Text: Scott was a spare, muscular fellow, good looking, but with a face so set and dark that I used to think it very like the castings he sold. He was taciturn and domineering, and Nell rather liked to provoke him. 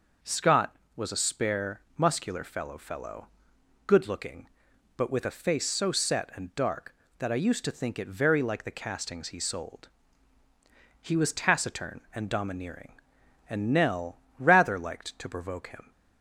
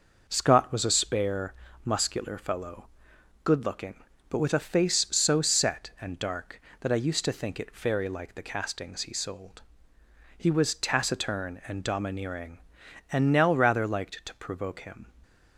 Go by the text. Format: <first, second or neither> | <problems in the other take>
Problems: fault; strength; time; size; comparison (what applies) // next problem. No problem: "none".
second | says "fellow" twice; at 2.7 s // pauses between "Nell" and "rather"; slight; at 14.1 s; 0.18 s long